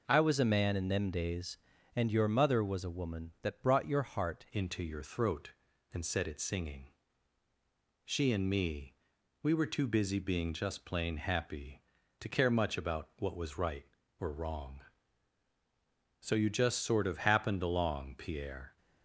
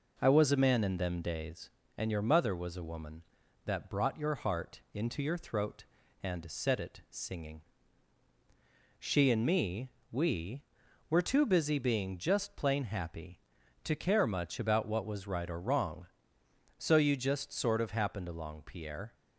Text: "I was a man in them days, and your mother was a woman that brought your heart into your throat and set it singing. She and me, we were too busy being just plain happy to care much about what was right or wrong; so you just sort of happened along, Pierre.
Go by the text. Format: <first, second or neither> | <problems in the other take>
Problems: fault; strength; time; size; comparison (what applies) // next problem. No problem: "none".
second | changes voice at "into"; from 4.5 s on; 14.2 s long